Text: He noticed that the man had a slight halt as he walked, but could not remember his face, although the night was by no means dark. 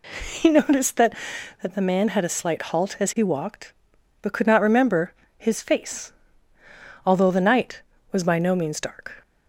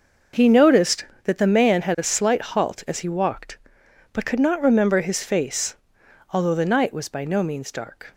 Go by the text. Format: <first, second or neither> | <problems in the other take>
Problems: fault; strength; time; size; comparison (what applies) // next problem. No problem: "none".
second | says "that" twice; at 1.6 s // pauses between "remember" and "his"; slight; at 5.1 s; 0.26 s long